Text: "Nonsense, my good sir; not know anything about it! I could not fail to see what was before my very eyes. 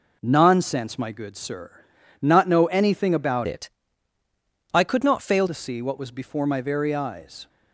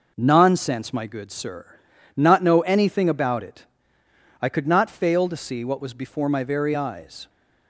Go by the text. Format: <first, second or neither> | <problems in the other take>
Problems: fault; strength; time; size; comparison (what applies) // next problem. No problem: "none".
second | changes voice from "it" to "fail"; from 3.4 to 5.4 s; 2.0 s long